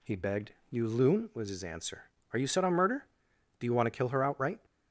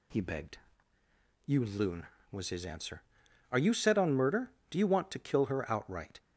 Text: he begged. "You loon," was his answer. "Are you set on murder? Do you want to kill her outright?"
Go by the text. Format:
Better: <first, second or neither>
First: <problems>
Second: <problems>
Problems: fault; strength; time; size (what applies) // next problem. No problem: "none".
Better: neither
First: none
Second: none